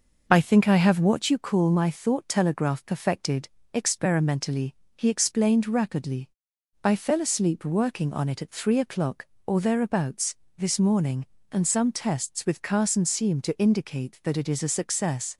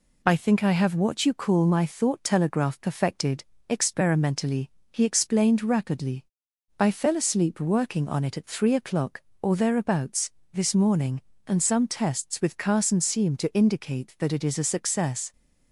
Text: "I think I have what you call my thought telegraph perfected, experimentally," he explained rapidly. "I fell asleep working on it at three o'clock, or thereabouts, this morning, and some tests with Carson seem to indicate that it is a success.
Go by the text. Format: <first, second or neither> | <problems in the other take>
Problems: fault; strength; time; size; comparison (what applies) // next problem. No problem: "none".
second | starts louder than the rest; noticeable; until 1.3 s; 6 dB